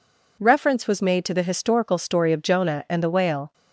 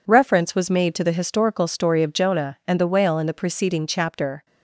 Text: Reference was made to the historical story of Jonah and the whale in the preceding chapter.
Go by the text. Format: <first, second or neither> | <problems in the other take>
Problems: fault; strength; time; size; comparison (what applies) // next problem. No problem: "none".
second | stops before "in the preceding chapter"; at 3.5 s